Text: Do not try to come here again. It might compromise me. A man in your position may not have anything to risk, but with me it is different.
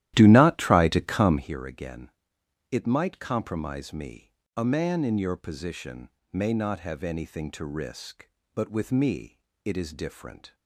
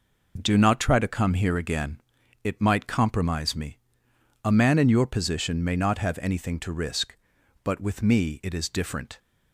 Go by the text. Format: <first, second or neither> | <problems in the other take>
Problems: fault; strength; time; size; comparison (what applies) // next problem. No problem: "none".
second | starts louder than the rest; strong; until 1.5 s; 13.5 dB // pauses between "position" and "may"; slight; at 6.0 s; 0.22 s long // pauses between "me" and "it"; slight; at 9.3 s; 0.26 s long